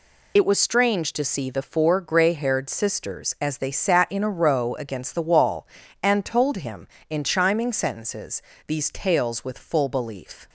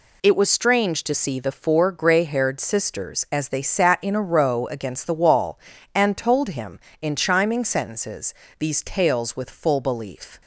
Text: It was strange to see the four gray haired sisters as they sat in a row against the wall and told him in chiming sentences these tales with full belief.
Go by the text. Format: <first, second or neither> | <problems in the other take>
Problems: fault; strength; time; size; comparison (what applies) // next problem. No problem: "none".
second | loses the start of "It"; at 0.3 s; 40 ms // pauses between "sentences" and "these"; slight; at 8.4 s; 0.24 s long; slight in the second